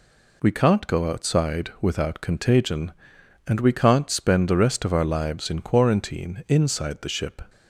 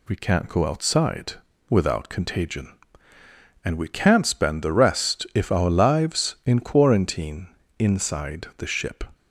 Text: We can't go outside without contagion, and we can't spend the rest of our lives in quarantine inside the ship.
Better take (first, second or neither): first